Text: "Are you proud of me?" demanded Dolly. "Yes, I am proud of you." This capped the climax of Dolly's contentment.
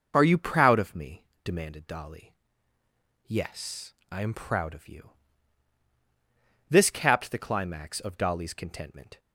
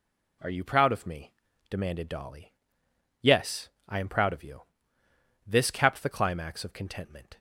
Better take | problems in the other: first | skips "Dolly's"; at 6.7 s

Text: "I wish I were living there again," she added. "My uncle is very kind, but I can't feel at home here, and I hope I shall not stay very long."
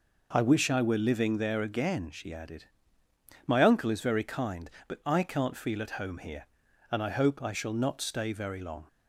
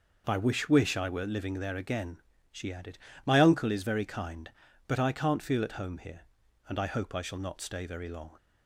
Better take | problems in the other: first | says "wish" twice; at 0.7 s

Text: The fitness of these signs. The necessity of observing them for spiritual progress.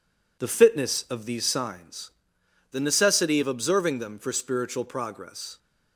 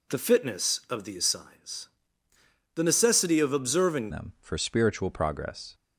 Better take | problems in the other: first | changes voice at "them"; from 4.1 s on; 1.6 s long

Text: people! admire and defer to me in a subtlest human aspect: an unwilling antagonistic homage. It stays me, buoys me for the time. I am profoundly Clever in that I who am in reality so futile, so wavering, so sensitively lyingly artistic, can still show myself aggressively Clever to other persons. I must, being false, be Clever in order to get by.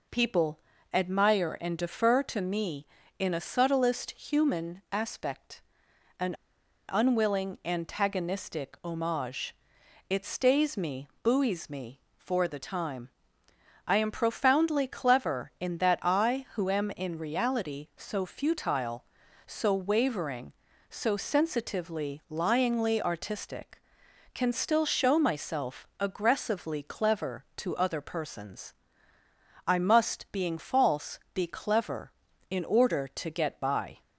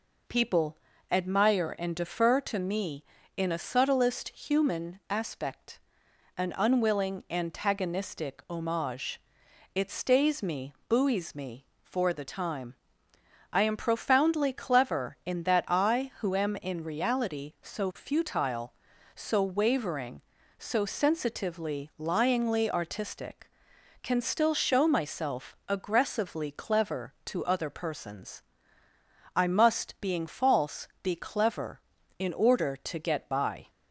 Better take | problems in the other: second | pauses between "an" and "unwilling"; noticeable; at 6.3 s; 0.56 s long

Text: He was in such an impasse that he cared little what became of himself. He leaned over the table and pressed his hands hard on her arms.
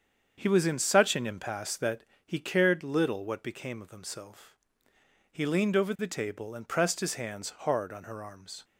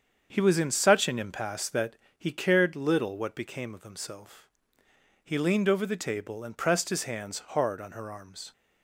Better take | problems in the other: neither | starts louder than the rest; strong; the same in both // pauses between "that" and "he"; slight; the same in both

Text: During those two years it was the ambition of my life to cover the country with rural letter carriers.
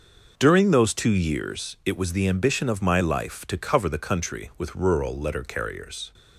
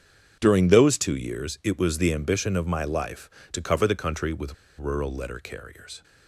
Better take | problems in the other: first | starts louder than the rest; strong; until 1.4 s; 7.5 dB; noticeable in the first // pauses between "with" and "rural"; slight; at 4.5 s; 0.24 s long

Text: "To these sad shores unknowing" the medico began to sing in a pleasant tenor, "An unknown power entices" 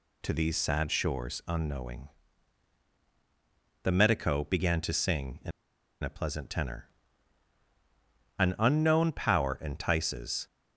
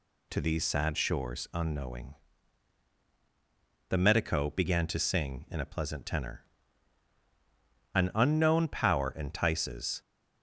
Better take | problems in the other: second | pauses between "unknowing" and "the"; strong; at 2.0 s; 1.7 s long; strong in the second // pauses between "in" and "a"; noticeable; at 5.5 s; 0.52 s long

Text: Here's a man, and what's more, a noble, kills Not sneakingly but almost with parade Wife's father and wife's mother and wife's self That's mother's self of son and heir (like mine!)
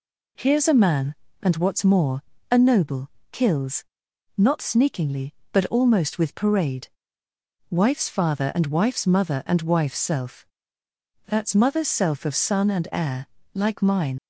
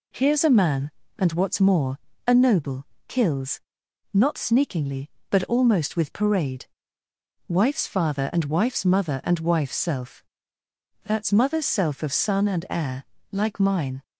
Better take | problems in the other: second | pauses between "kills" and "Not"; noticeable; at 3.8 s; 0.52 s long; noticeable in the second // pauses between "parade" and "Wife's"; noticeable; at 6.8 s; 0.82 s long; noticeable in the second // pauses between "self" and "That's"; noticeable; at 10.4 s; 0.80 s long; noticeable in the second // leaves "mine" unfinished; at 14.1 s; 65 ms

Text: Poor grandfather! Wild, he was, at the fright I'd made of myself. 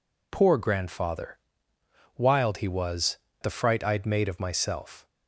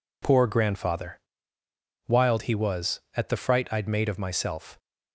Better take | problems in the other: second | skips "at"; at 3.2 s

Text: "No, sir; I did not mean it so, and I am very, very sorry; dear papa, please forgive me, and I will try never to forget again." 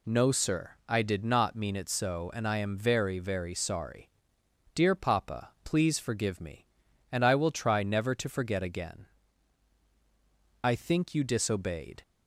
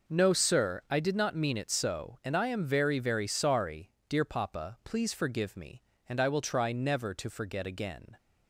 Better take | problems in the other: second | goes on to say "I think you disobeyed"; from 10.6 s on; 1.3 s long

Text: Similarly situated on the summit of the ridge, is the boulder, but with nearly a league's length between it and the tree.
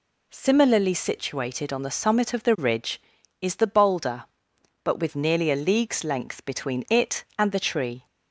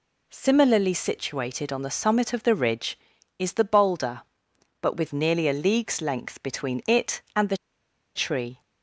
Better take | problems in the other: first | pauses between "the" and "tree"; noticeable; at 7.5 s; 0.58 s long

